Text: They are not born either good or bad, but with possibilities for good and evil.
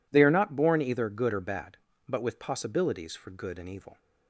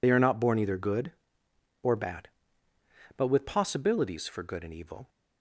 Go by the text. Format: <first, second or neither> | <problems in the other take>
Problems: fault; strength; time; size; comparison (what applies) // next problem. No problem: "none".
first | loses the start of "They"; at 0.0 s; 30 ms